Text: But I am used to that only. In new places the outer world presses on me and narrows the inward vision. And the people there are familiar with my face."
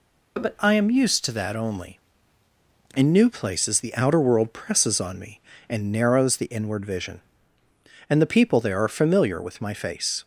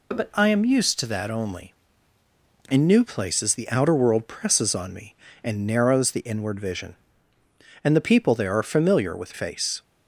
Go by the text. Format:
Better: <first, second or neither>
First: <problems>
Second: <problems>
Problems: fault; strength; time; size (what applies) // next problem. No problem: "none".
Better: first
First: none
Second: skips "my"; at 9.3 s